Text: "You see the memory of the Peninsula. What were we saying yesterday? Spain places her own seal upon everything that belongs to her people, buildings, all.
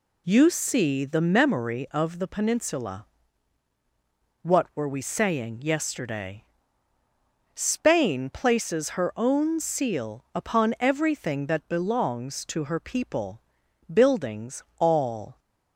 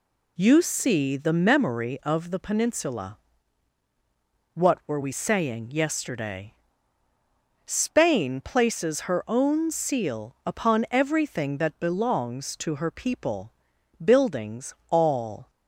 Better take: neither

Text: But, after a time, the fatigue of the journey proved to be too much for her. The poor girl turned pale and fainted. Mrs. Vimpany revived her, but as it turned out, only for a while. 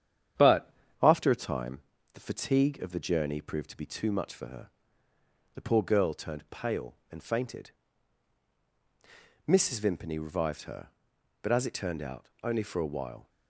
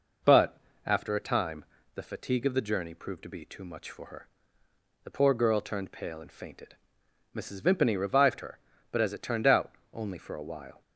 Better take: second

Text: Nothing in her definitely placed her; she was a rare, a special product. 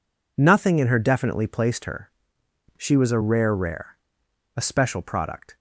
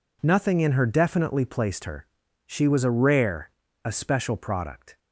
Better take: second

